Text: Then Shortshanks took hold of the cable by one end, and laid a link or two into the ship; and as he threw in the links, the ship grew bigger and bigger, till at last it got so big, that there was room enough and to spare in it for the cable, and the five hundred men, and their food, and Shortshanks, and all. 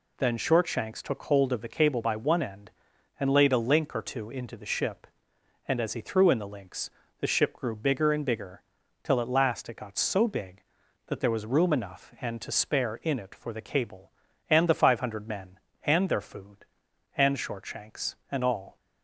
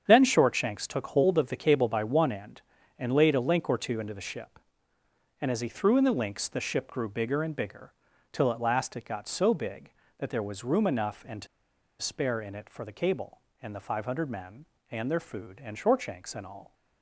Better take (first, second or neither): first